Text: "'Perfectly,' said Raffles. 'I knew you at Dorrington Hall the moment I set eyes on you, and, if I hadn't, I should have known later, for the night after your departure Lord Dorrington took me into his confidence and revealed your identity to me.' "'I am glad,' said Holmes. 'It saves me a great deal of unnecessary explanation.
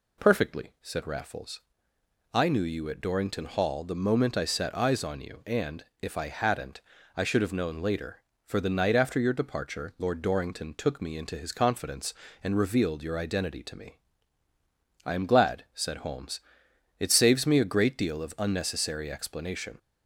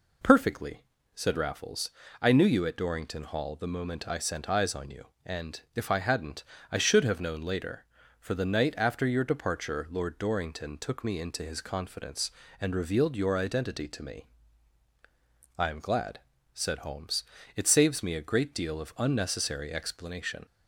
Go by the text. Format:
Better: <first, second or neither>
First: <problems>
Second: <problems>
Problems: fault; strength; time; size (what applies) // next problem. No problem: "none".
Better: first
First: none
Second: says "sent" for "set"; at 4.1 s